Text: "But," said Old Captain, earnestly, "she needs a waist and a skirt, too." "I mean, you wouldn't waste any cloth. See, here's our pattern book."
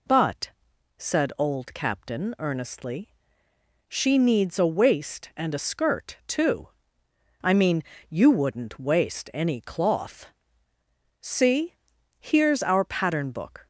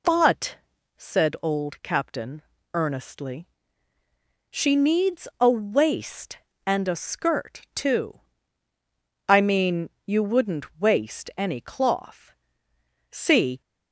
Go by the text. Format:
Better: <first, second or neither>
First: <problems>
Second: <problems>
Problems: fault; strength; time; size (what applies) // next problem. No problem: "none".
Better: first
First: none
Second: stops before "here's our pattern book"; at 13.6 s